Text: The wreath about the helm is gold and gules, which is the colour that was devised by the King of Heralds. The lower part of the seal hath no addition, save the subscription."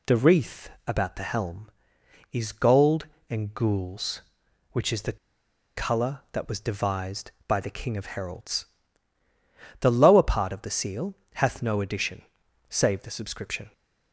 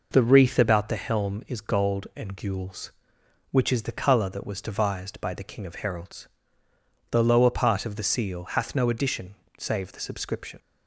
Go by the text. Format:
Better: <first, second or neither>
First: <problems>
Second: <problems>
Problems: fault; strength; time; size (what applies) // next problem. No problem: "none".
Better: second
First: pauses between "wreath" and "about"; slight; at 0.6 s; 0.18 s long // pauses between "the" and "colour"; noticeable; at 5.1 s; 0.59 s long // pauses between "seal" and "hath"; slight; at 11.1 s; 0.20 s long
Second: none